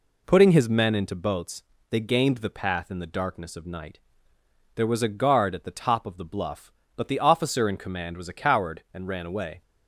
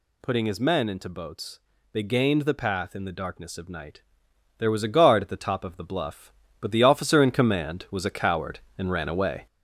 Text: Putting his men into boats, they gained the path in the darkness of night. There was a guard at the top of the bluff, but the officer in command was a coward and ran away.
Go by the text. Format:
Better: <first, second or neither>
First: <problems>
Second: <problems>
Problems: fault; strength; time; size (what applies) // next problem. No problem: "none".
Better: first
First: none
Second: gets louder; throughout; 4 dB